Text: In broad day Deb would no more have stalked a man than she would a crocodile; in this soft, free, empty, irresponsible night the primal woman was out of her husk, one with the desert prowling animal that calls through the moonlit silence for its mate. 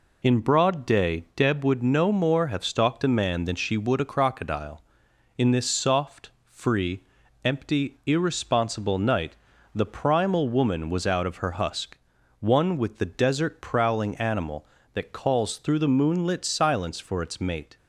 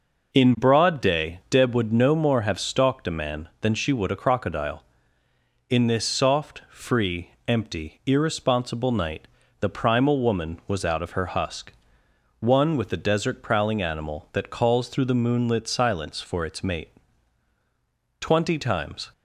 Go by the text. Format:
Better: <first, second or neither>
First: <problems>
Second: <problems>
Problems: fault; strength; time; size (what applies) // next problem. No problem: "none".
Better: first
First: pauses between "night" and "the"; at 9.3 s; 0.40 s long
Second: pauses between "night" and "the"; slight; at 9.2 s; 0.32 s long // goes on to say "Twenty times"; noticeable; from 18.1 s on; 0.92 s long